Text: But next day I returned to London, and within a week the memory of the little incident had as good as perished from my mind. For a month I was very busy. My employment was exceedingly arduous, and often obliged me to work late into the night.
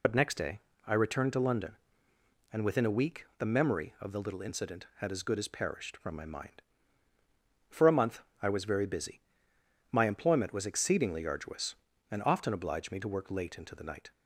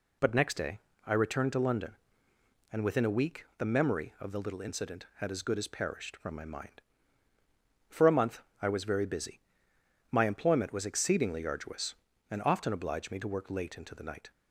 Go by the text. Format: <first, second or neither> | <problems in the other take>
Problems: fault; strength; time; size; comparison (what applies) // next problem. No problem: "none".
second | loses the start of "But"; at 0.0 s; 40 ms // pauses between "day" and "I"; slight; at 0.5 s; 0.28 s long; slight in the second // pauses between "month" and "I"; slight; at 8.2 s; 0.20 s long; slight in the second